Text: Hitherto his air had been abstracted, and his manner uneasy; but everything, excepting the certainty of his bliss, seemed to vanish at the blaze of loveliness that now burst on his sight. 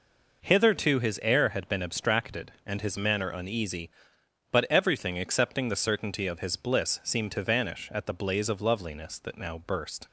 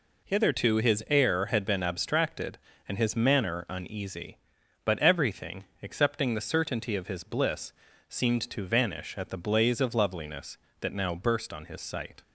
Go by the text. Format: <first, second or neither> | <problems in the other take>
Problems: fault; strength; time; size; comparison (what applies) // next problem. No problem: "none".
second | stops before "on his sight"; at 10.0 s